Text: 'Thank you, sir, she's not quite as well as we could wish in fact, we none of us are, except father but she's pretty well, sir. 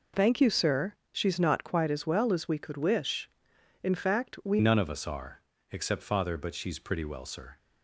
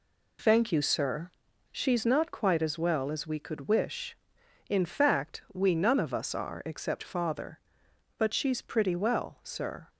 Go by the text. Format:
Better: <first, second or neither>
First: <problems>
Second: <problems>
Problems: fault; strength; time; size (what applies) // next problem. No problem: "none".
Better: second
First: changes voice at "none"; from 4.5 s on; 3.0 s long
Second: none